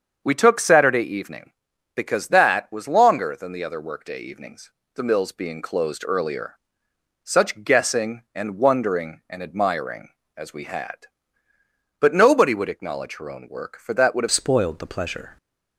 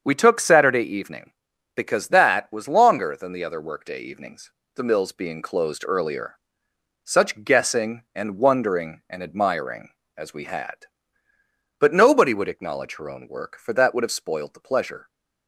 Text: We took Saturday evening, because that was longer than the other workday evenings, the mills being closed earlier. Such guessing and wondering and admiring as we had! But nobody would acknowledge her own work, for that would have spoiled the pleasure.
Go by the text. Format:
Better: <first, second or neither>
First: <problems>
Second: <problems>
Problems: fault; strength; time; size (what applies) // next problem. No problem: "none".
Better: second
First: starts louder than the rest; until 1.2 s; 7 dB // changes voice at "spoiled"; from 14.3 s on; 1.0 s long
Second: starts louder than the rest; until 1.0 s; 7 dB